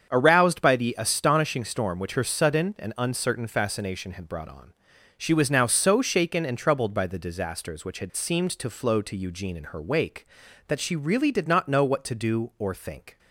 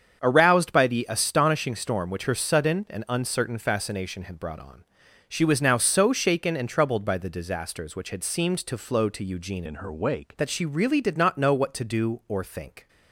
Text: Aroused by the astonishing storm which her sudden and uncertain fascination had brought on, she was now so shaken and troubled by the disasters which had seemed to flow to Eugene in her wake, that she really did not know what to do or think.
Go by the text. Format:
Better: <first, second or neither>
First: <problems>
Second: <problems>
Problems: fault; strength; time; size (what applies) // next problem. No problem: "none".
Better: first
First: starts louder than the rest; strong; until 1.1 s; 7.5 dB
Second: starts louder than the rest; strong; until 1.2 s; 7.5 dB // changes voice from "in" to "wake"; from 9.6 to 10.3 s; 0.7 s long